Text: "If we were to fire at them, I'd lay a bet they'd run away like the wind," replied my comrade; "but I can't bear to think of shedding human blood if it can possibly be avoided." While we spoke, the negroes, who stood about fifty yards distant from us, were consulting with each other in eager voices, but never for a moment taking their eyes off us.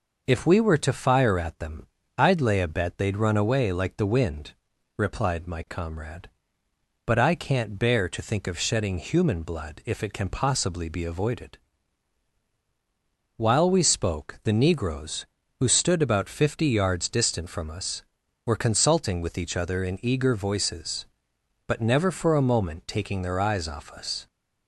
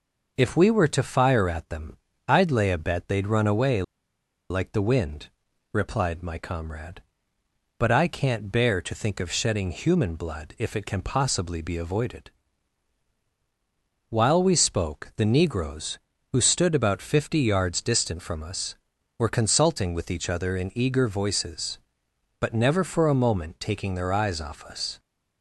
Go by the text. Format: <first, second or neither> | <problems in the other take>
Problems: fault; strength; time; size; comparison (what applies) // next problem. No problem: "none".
first | pauses between "away" and "like"; noticeable; at 3.8 s; 0.68 s long